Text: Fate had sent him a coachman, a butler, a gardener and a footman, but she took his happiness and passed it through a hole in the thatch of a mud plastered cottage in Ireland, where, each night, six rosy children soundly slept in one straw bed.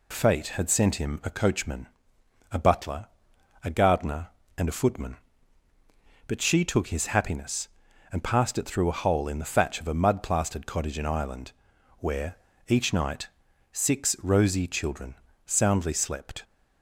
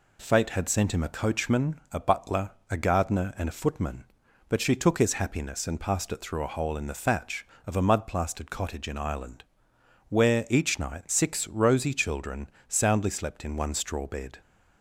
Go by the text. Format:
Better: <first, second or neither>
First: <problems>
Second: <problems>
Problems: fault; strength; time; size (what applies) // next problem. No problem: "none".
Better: second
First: pauses between "children" and "soundly"; slight; at 15.1 s; 0.30 s long // stops before "in one straw bed"; at 16.4 s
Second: pauses between "children" and "soundly"; slight; at 12.4 s; 0.20 s long